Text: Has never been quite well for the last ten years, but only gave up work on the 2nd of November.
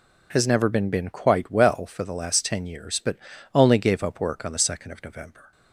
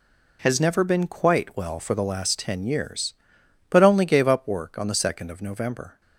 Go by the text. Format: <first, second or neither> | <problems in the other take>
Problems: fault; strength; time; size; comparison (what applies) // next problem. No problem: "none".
second | says "been" twice; at 0.8 s // pauses between "but" and "only"; slight; at 3.1 s; 0.36 s long